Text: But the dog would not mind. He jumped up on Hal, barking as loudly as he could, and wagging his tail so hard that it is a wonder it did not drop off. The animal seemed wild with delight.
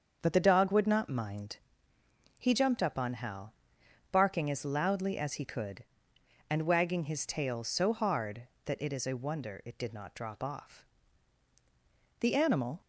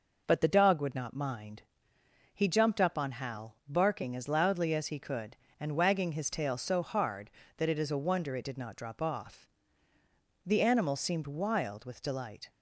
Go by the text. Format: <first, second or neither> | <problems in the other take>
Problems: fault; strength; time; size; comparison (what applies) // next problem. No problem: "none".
second | starts louder than the rest; until 1.2 s; 7 dB // stops before "seemed wild with delight"; at 12.8 s